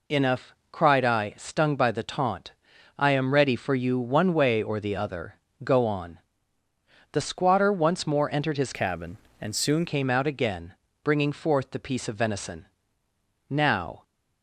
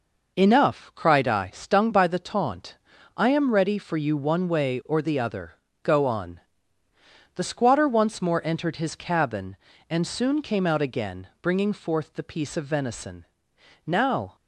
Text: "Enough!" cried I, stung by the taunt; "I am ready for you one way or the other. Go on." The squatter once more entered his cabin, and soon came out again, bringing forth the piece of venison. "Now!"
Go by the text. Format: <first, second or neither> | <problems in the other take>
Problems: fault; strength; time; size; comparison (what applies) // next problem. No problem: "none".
second | changes voice from "cabin" to "soon"; from 8.7 to 9.8 s; 1.1 s long